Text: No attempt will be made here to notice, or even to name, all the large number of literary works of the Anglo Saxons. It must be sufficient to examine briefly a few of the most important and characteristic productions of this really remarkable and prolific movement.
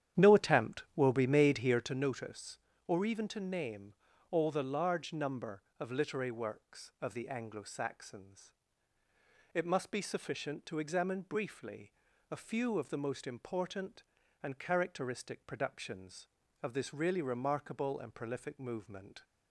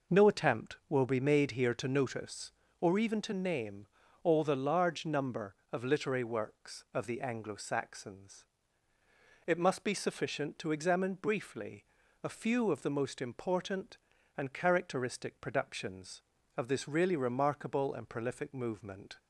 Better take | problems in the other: second | starts louder than the rest; strong; until 2.0 s; 10 dB // pauses between "briefly" and "a"; at 11.9 s; 0.40 s long; also in the second

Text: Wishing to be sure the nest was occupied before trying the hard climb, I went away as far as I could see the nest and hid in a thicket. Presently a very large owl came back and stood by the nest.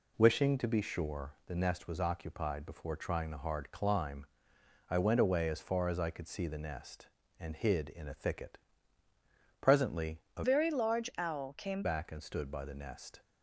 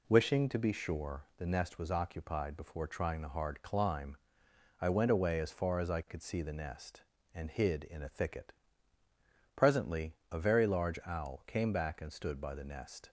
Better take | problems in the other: second | pauses between "Presently" and "a"; slight; at 10.1 s; 0.16 s long; slight in the second // changes voice from "very" to "came"; from 10.4 to 11.8 s; 1.4 s long

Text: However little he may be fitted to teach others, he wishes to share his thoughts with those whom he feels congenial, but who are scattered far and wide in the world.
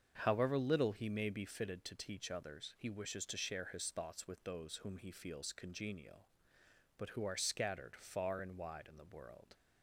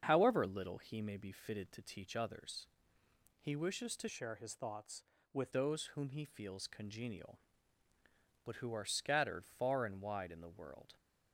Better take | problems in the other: first | starts louder than the rest; until 1.0 s; 7 dB; also in the first // changes voice from "share" to "with"; from 4.0 to 5.5 s; 1.5 s long

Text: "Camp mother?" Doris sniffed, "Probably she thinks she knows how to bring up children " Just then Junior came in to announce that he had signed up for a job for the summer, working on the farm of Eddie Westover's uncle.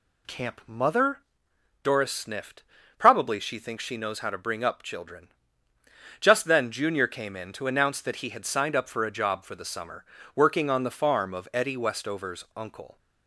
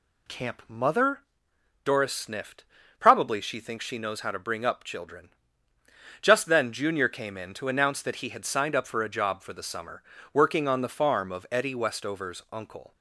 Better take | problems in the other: neither | none

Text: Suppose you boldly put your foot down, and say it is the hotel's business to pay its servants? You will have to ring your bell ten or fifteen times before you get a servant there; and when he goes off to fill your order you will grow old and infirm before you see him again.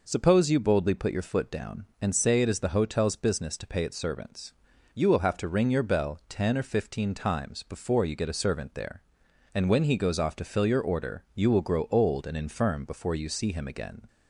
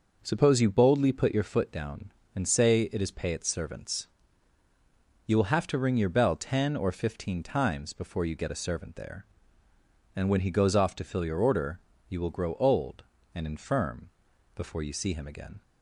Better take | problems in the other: first | skips "the hotel's business to"; at 3.1 s // pauses between "order" and "you"; slight; at 11.7 s; 0.30 s long // pauses between "infirm" and "before"; noticeable; at 14.0 s; 0.46 s long

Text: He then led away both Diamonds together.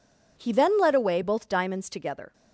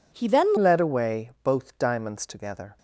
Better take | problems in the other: first | changes voice at "led"; from 0.5 s on; 2.2 s long

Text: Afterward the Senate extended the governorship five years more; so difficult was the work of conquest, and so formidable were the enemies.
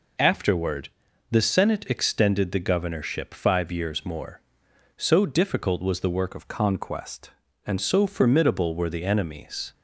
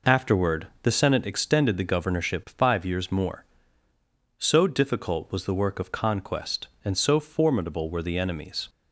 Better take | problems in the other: second | pauses between "Afterward" and "the"; at 0.8 s; 0.42 s long; slight in the second // changes voice from "of" to "and"; from 6.3 to 7.7 s; 1.4 s long

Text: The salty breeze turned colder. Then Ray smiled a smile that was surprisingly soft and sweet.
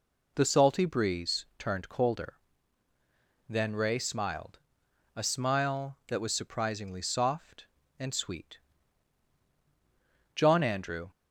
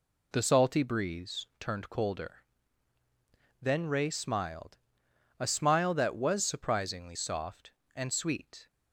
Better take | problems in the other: second | pauses between "smiled" and "a"; noticeable; at 4.5 s; 0.58 s long; noticeable in the second // goes on to say "John Andrew"; noticeable; from 10.3 s on; 0.74 s long

